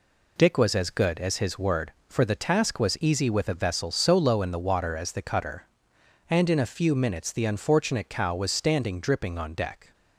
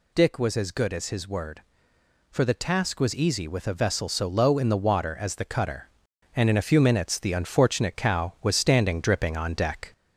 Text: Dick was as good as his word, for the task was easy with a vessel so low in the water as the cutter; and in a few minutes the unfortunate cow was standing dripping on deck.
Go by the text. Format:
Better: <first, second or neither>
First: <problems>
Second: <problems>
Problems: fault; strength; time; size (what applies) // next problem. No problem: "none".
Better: first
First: none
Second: gets louder; slight; throughout; 2.5 dB